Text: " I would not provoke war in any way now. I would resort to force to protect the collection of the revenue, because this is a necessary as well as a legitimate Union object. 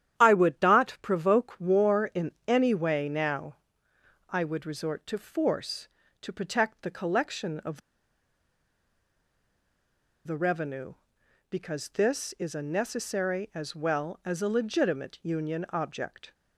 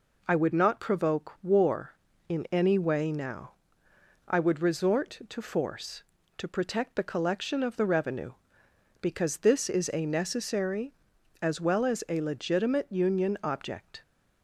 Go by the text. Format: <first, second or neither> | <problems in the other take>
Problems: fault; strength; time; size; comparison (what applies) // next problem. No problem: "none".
second | starts louder than the rest; strong; until 1.2 s; 10.5 dB // pauses between "in" and "any"; slight; at 2.3 s; 0.16 s long // pauses between "of" and "the"; strong; at 7.8 s; 2.4 s long